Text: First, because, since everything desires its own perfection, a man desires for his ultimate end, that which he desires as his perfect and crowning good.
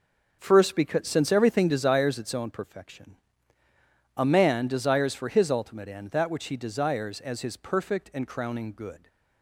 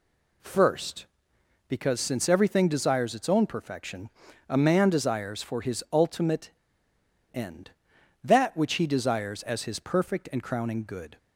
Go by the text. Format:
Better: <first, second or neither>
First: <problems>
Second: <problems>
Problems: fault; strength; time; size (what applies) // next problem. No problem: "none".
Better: first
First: none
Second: pauses between "ultimate" and "end"; noticeable; at 6.4 s; 0.84 s long